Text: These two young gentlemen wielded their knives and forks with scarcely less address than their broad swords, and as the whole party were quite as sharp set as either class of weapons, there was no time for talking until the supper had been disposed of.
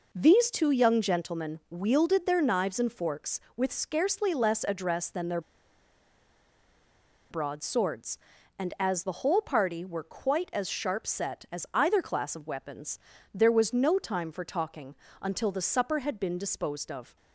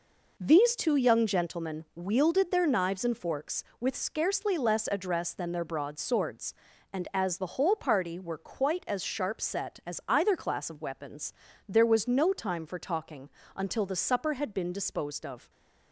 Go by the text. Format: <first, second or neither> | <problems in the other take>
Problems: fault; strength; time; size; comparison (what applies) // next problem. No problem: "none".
second | pauses between "their" and "broad"; strong; at 5.3 s; 1.9 s long // pauses between "talking" and "until"; slight; at 14.9 s; 0.30 s long; slight in the second